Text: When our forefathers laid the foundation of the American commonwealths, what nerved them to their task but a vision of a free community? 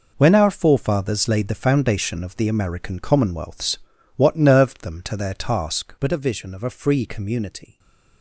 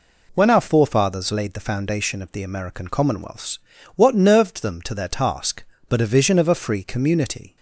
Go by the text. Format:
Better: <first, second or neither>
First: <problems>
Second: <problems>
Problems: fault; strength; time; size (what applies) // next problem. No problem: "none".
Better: neither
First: none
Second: none